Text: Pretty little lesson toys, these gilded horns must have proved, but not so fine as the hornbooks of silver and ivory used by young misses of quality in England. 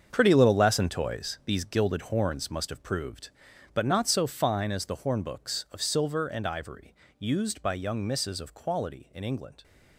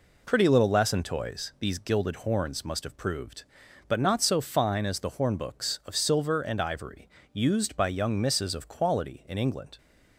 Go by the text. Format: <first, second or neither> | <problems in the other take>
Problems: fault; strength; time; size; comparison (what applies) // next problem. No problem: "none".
second | gets quieter; strong; throughout; 11 dB // pauses between "ivory" and "used"; slight; at 6.9 s; 0.24 s long; slight in the second